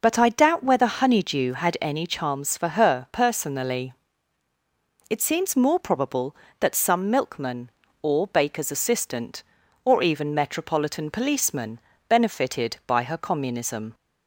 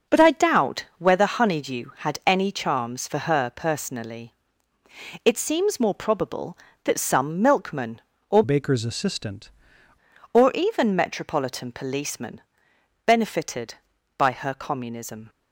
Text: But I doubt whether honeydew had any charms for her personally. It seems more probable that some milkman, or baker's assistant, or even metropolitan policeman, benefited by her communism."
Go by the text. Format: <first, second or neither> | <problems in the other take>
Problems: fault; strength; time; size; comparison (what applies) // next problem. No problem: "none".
first | changes voice from "baker's" to "assistant"; from 8.4 to 9.4 s; 1.0 s long